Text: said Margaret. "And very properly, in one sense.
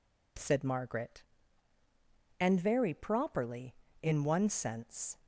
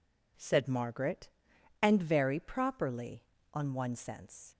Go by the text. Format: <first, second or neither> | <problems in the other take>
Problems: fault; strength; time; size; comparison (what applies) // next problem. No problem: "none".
first | says "on" for "in"; at 3.5 s